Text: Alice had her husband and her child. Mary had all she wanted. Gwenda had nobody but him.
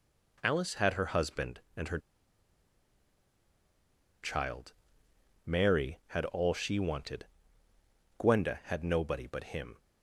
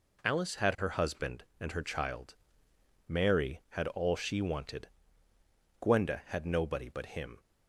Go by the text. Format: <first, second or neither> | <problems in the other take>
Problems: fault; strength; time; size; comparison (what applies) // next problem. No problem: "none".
second | pauses between "her" and "child"; strong; at 1.9 s; 2.2 s long